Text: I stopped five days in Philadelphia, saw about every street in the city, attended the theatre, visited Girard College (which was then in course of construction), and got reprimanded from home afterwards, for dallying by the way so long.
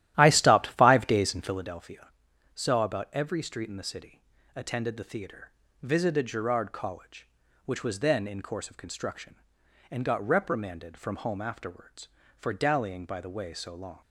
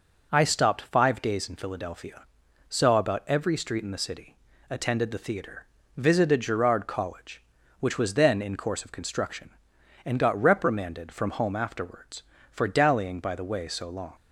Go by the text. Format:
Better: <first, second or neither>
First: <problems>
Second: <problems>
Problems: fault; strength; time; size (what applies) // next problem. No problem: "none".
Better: second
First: starts louder than the rest; strong; until 1.8 s; 13.5 dB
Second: none